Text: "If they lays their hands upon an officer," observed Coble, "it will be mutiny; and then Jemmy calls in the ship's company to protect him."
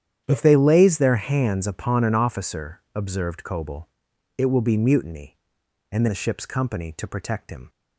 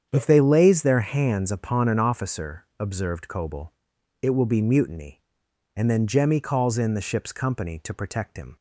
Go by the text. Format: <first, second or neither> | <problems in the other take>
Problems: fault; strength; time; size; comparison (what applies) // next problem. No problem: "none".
second | starts louder than the rest; strong; until 1.2 s; 9.5 dB; strong in the second // skips "then Jemmy calls in"; at 6.0 s